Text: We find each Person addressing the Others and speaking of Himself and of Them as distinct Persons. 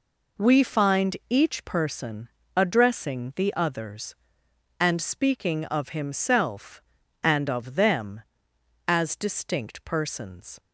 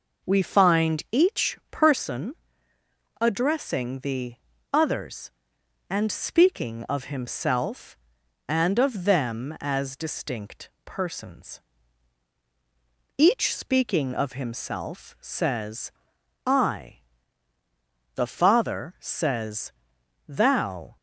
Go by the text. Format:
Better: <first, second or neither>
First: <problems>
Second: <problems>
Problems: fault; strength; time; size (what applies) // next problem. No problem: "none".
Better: first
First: pauses between "Person" and "addressing"; slight; at 2.2 s; 0.30 s long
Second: pauses between "Person" and "addressing"; noticeable; at 2.3 s; 0.86 s long // pauses between "the" and "Others"; at 4.3 s; 0.38 s long // pauses between "distinct" and "Persons"; slight; at 10.6 s; 0.16 s long // goes on to say "Each speaking of Himself says I The Father says Thou"; strong; from 13.1 s on; 7.7 s long